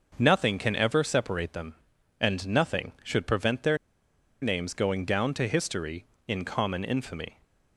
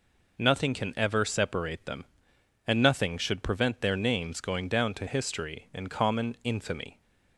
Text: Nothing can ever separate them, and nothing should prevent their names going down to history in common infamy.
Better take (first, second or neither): second